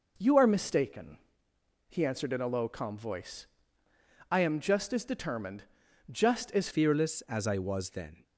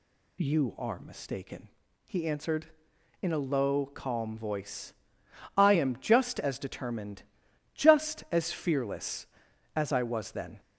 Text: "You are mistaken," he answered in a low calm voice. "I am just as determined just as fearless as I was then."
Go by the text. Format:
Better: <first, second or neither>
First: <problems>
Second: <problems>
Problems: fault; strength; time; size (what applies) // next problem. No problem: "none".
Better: second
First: pauses between "determined" and "just"; at 5.6 s; 0.44 s long // changes voice at "fearless"; from 6.7 s on; 1.5 s long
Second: pauses between "determined" and "just"; noticeable; at 7.2 s; 0.50 s long